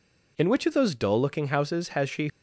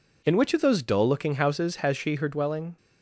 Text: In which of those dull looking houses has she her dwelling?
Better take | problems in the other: second | stops before "her dwelling"; at 2.2 s

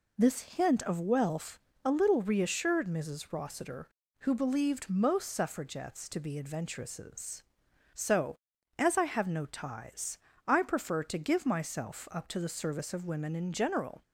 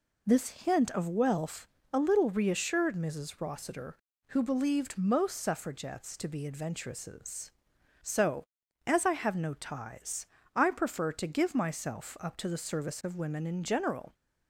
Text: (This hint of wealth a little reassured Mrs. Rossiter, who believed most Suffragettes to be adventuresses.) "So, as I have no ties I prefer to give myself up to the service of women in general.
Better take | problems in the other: neither | pauses between "wealth" and "a"; slight; the same in both // pauses between "ties" and "I"; slight; the same in both

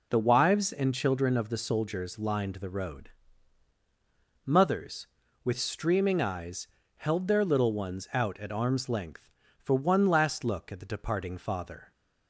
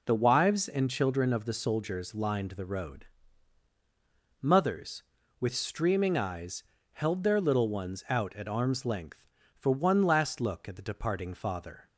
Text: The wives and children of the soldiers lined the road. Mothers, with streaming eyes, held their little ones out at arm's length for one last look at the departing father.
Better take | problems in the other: neither | none

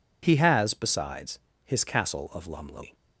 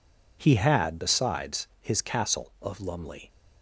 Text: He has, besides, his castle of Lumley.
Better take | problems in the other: first | says "had" for "has"; at 0.5 s

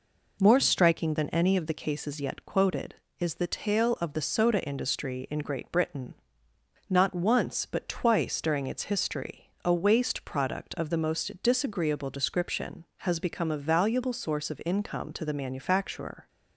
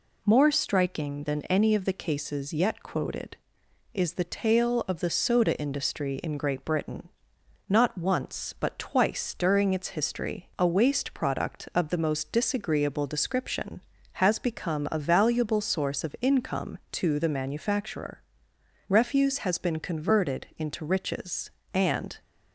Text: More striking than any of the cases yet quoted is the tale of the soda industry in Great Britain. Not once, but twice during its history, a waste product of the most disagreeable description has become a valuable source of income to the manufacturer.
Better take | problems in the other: first | goes on to say "Refuse has been converted into riches and"; strong; from 18.8 s on; 3.3 s long

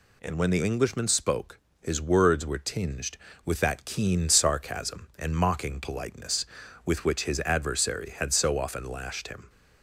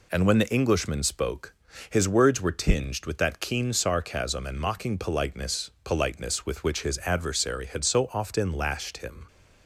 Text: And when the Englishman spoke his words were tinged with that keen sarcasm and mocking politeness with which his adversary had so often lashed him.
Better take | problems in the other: first | pauses between "spoke" and "his"; at 1.5 s; 0.38 s long; slight in the first // says "politeness" twice; at 5.8 s

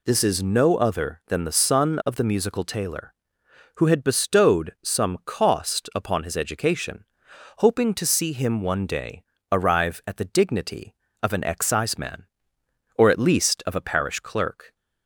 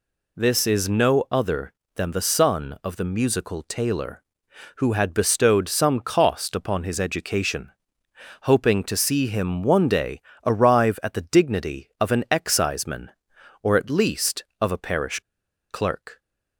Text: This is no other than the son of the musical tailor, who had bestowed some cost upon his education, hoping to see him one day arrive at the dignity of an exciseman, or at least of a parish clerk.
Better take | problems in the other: first | pauses between "day" and "arrive"; slight; at 10.2 s; 0.26 s long; slight in the first // pauses between "parish" and "clerk"; noticeable; at 15.1 s; 0.51 s long

